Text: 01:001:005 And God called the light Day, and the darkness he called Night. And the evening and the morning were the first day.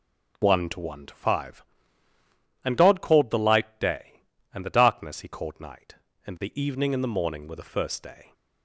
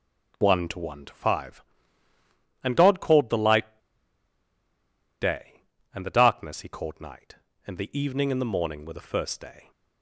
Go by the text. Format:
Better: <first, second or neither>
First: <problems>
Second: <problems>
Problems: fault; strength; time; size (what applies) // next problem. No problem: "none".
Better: first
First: none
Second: pauses between "light" and "Day"; strong; at 3.7 s; 1.4 s long